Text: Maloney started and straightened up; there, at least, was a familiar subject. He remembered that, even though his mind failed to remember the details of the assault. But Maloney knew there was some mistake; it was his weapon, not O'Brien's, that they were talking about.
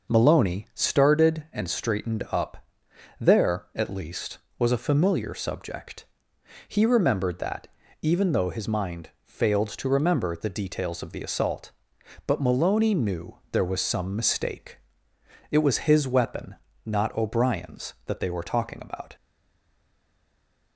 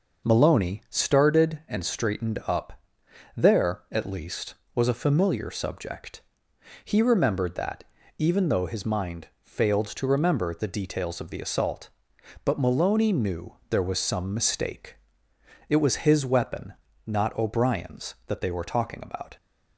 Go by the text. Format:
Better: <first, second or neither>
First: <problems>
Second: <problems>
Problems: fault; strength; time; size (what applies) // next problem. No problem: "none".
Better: second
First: stays silent after the last word; noticeable; from 19.1 s on; 1.6 s long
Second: none